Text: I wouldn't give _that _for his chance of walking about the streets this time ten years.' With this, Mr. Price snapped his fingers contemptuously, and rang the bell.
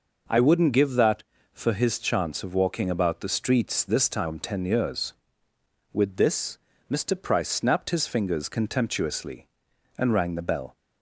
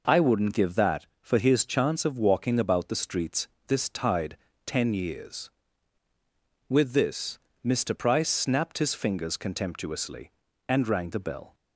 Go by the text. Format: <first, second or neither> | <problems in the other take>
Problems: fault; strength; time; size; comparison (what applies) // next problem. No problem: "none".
first | pauses between "streets" and "this"; slight; at 3.4 s; 0.18 s long // says "tide" for "time"; at 3.8 s